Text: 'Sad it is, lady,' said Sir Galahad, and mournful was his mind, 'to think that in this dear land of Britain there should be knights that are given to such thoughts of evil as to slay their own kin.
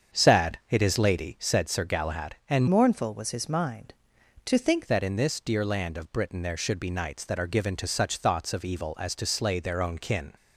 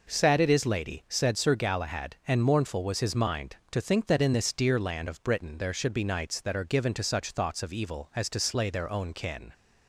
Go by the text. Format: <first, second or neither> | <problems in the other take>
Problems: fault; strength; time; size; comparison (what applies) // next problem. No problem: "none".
second | starts louder than the rest; strong; until 1.2 s; 7.5 dB // changes voice from "mournful" to "think"; from 2.6 to 4.8 s; 2.2 s long